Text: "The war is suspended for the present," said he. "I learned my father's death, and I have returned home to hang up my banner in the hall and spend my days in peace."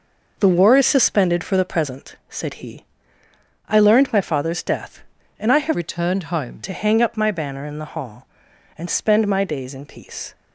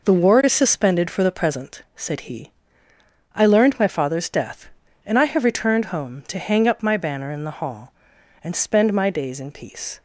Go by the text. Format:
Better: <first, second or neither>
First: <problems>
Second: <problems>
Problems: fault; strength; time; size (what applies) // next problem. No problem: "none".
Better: second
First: changes voice from "returned" to "home"; from 5.7 to 6.6 s; 0.9 s long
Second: none